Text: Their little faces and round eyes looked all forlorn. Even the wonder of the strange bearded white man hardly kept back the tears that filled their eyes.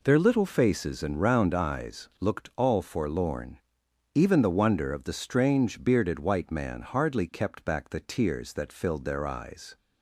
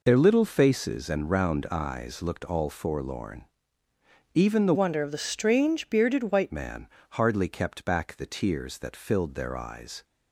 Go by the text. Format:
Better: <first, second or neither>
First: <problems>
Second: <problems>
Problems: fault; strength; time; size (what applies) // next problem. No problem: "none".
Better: first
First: none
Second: changes voice from "wonder" to "white"; from 4.7 to 6.5 s; 1.8 s long // pauses between "man" and "hardly"; slight; at 6.8 s; 0.24 s long